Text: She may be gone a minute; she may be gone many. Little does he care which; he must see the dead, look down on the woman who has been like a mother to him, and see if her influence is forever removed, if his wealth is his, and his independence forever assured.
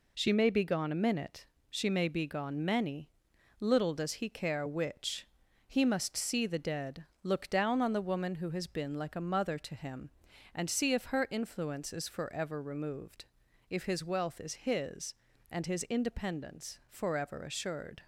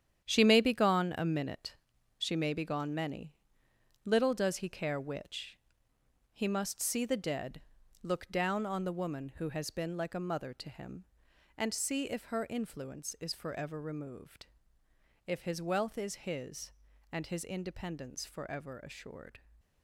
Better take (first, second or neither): first